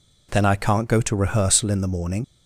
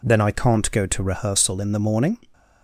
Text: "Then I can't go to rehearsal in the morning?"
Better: second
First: leaves "morning" unfinished; at 2.2 s; 55 ms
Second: none

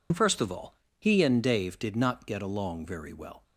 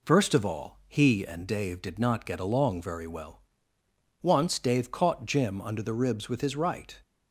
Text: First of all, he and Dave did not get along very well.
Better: first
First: none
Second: goes on to say "Once Dave caught Jim under the ribs with his right"; strong; from 4.2 s on; 2.7 s long

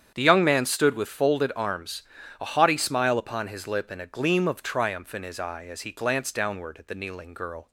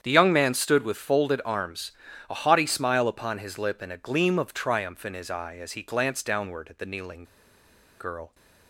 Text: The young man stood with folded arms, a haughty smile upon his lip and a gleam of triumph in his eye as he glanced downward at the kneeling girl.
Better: first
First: starts louder than the rest; strong; until 1.1 s; 8.5 dB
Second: starts louder than the rest; strong; until 1.0 s; 8.5 dB // pauses between "kneeling" and "girl"; noticeable; at 7.2 s; 0.76 s long

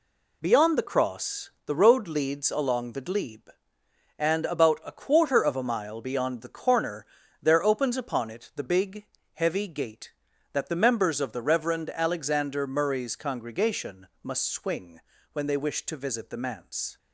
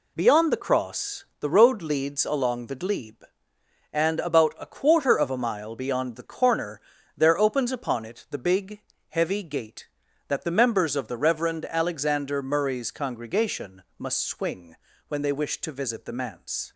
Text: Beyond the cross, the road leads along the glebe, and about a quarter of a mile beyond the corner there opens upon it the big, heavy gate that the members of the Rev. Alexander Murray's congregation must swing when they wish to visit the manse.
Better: neither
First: pauses between "corner" and "there"; slight; at 7.0 s; 0.36 s long // pauses between "congregation" and "must"; slight; at 14.0 s; 0.16 s long // pauses between "swing" and "when"; slight; at 14.9 s; 0.32 s long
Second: pauses between "corner" and "there"; slight; at 6.8 s; 0.36 s long // pauses between "congregation" and "must"; slight; at 13.8 s; 0.16 s long // pauses between "swing" and "when"; slight; at 14.7 s; 0.32 s long

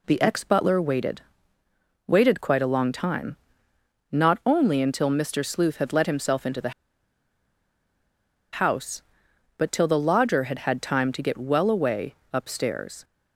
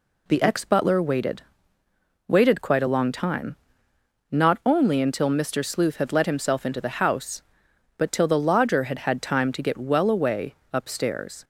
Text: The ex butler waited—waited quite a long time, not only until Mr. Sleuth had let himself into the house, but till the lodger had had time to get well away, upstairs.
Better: second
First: pauses between "the" and "house"; strong; at 6.7 s; 1.8 s long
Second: none

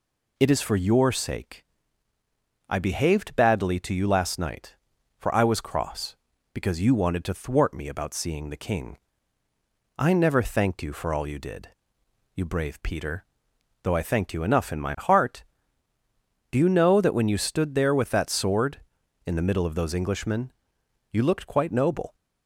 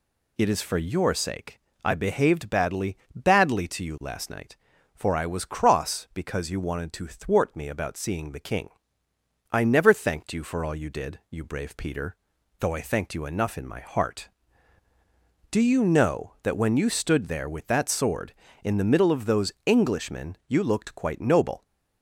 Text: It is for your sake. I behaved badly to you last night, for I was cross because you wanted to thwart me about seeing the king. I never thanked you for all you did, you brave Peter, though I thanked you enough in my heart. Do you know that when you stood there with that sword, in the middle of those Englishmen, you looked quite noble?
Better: first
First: none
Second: says "badly" twice; at 3.1 s

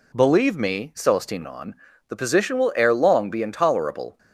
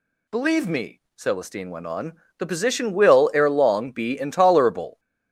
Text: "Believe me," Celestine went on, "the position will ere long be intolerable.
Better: second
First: skips "went"; at 1.4 s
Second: none

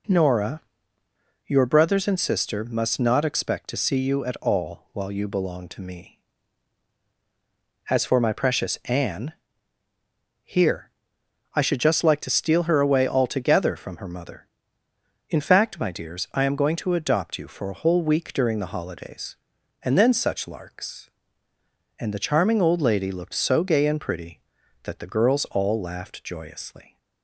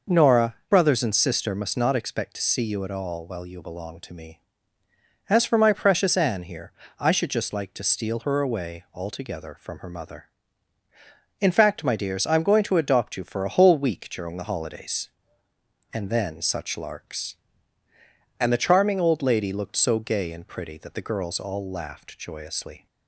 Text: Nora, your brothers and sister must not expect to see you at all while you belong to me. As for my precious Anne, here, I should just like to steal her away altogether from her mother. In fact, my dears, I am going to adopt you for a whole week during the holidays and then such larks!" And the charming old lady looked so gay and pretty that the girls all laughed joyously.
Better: first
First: none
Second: skips "your"; at 0.6 s

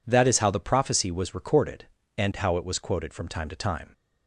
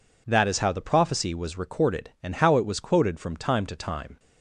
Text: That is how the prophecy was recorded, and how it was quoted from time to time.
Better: neither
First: none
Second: none

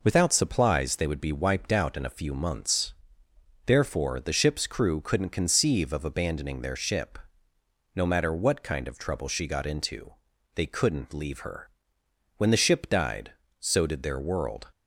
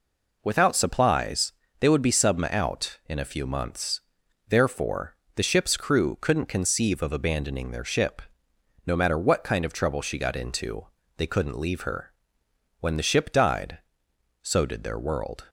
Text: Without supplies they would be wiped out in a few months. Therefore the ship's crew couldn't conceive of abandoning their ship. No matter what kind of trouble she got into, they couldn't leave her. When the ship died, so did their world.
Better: first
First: none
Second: pauses between "supplies" and "they"; slight; at 1.5 s; 0.28 s long // says "subma" for "wiped"; at 2.1 s // pauses between "Therefore" and "the"; slight; at 5.1 s; 0.20 s long

